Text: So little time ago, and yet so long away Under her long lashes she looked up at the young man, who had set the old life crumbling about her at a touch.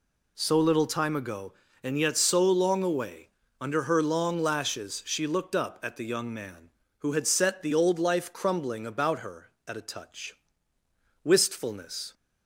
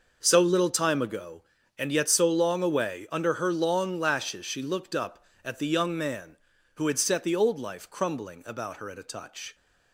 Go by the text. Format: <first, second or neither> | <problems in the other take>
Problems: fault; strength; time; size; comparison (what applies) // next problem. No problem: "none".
second | pauses between "away" and "Under"; slight; at 3.2 s; 0.32 s long // goes on to say "Wistfulness"; noticeable; from 11.2 s on; 0.90 s long